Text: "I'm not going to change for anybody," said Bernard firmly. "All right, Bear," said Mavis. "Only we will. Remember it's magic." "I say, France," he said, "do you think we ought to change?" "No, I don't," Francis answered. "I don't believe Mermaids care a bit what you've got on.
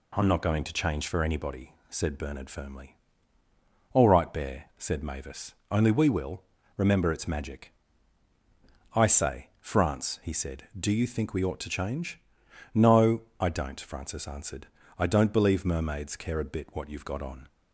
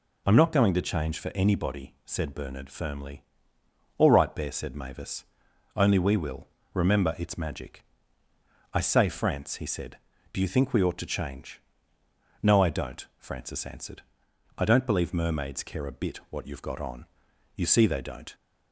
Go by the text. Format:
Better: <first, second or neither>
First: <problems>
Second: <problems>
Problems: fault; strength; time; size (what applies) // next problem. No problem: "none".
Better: first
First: none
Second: goes on to say "You see they don't"; noticeable; from 17.5 s on; 0.78 s long